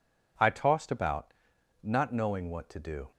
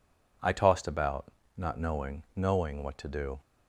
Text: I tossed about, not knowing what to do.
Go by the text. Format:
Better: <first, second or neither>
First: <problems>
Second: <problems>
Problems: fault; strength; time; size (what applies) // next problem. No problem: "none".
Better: first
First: none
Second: says "knowing" twice; at 2.3 s